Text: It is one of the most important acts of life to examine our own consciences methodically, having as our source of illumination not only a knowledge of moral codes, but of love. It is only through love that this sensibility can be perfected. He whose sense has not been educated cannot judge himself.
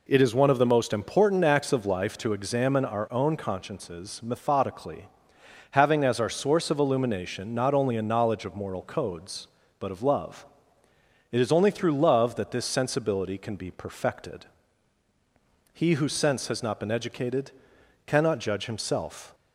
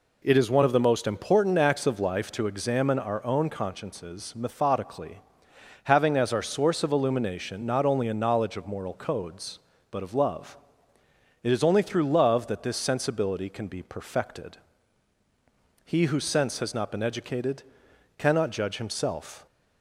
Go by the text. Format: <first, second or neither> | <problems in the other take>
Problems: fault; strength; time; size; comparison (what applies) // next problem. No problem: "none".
neither | pauses between "educated" and "cannot"; noticeable; the same in both